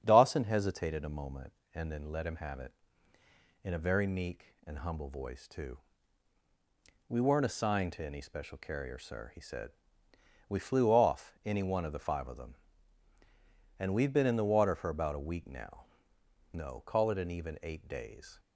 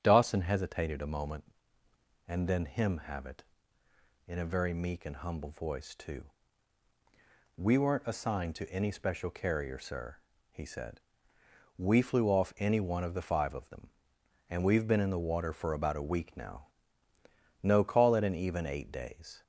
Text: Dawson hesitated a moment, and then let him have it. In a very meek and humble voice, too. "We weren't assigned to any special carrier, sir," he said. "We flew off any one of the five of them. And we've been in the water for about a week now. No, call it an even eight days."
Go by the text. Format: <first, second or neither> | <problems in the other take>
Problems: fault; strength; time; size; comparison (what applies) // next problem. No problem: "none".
first | starts louder than the rest; strong; until 1.0 s; 8.5 dB; strong in the first // skips "let"; at 2.6 s